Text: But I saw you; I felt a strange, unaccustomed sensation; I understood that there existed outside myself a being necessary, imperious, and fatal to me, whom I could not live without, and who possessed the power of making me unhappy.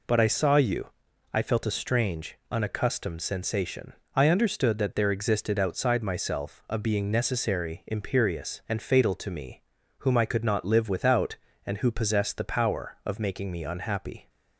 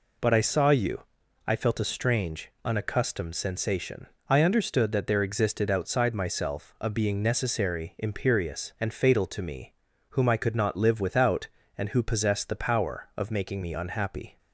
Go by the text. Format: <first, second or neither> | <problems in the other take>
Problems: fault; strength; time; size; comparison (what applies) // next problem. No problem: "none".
neither | none